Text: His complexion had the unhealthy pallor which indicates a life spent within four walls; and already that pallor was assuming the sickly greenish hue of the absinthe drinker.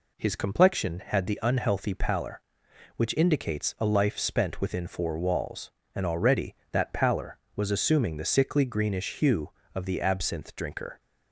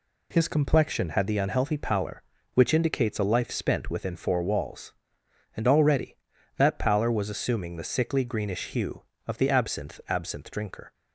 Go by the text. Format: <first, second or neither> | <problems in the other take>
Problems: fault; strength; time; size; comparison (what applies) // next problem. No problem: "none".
first | says "absinthe" twice; at 10.0 s